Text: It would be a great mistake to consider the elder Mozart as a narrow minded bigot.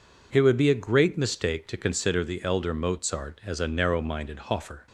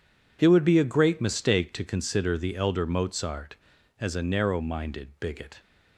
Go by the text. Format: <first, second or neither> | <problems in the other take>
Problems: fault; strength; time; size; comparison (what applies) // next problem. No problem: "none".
second | says "hoffer" for "bigot"; at 4.3 s